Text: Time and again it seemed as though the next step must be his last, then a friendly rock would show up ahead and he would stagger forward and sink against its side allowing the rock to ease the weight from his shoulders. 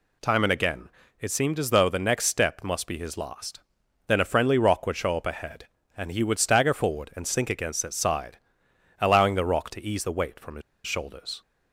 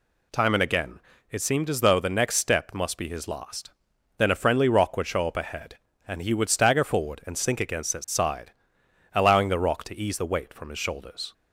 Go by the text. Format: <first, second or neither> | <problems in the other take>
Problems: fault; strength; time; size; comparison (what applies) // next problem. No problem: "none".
second | pauses between "again" and "it"; slight; at 0.8 s; 0.30 s long; slight in the second // pauses between "side" and "allowing"; noticeable; at 8.3 s; 0.62 s long; noticeable in the second // pauses between "his" and "shoulders"; slight; at 10.6 s; 0.25 s long